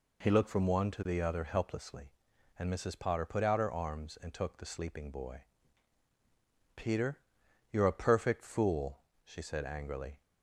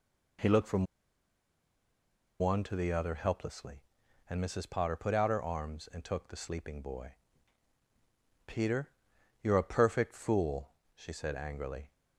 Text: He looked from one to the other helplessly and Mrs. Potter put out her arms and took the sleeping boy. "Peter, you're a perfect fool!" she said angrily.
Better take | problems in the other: first | pauses between "from" and "one"; strong; at 0.8 s; 1.5 s long

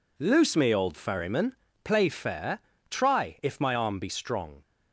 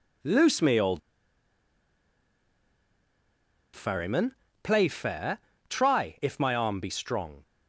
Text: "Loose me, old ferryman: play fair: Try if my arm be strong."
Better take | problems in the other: first | pauses between "old" and "ferryman"; strong; at 1.0 s; 2.7 s long

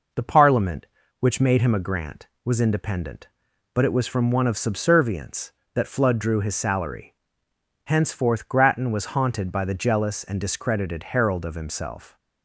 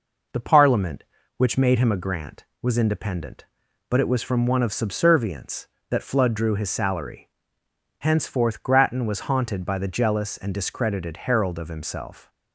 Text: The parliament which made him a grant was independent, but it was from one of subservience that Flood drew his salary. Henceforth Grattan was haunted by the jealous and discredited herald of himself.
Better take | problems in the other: neither | none

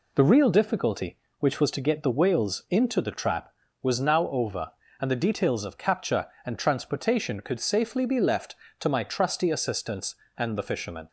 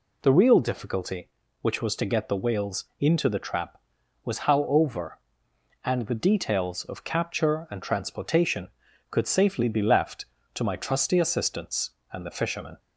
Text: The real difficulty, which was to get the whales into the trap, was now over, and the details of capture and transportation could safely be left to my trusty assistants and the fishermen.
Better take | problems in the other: first | says "how" for "now"; at 4.3 s

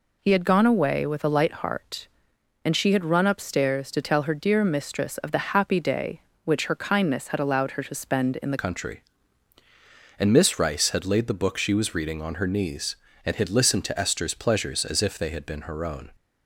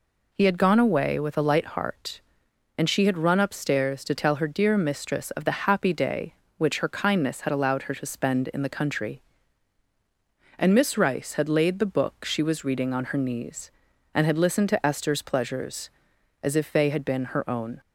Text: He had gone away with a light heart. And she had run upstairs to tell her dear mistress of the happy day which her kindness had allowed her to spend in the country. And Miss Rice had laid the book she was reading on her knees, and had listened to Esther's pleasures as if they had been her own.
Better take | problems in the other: second | changes voice at "country"; from 8.5 s on; 7.6 s long

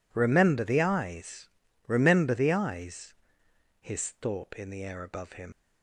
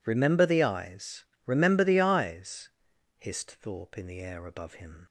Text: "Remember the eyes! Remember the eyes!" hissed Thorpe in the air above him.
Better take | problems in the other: second | leaves "him" unfinished; at 5.5 s; 120 ms

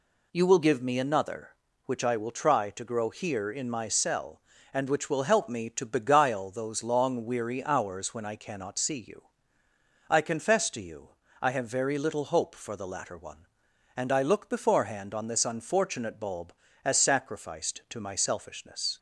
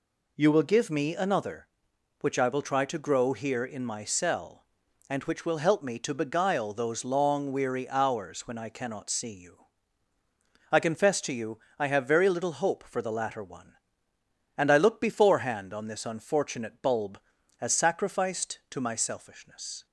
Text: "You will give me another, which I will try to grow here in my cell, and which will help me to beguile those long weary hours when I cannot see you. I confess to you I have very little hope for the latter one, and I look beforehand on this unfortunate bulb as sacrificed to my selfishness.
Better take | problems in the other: neither | pauses between "you" and "I"; slight; the same in both

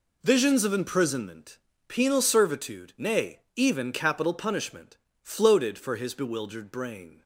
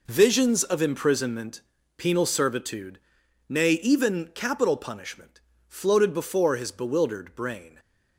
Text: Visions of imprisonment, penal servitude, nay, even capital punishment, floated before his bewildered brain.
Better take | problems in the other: second | says "for" for "before"; at 5.7 s

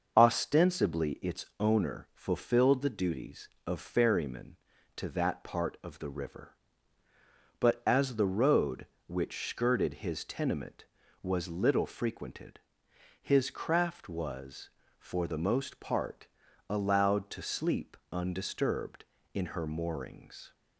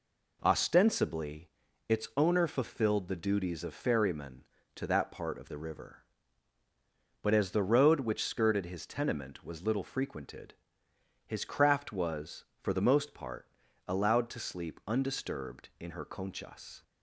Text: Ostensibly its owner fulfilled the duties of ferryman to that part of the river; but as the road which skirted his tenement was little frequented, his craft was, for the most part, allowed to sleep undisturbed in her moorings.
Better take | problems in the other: first | pauses between "Ostensibly" and "its"; slight; at 1.5 s; 0.36 s long // says "conchas" for "moorings"; at 16.0 s

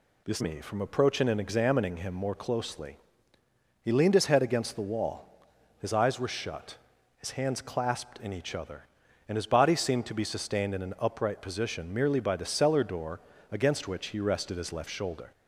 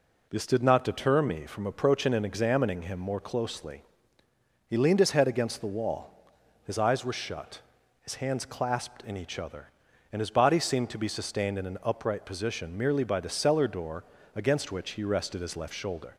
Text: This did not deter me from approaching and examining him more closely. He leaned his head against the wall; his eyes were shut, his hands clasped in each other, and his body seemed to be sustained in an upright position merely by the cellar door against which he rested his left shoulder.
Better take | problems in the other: second | skips "did not deter"; at 0.4 s // pauses between "door" and "against"; slight; at 13.1 s; 0.32 s long; slight in the second

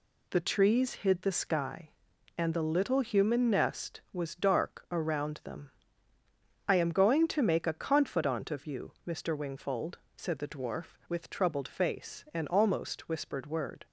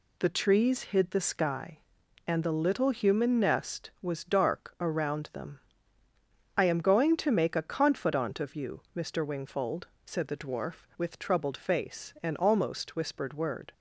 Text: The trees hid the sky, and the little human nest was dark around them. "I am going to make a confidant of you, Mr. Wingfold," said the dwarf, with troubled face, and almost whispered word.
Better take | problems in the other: neither | none

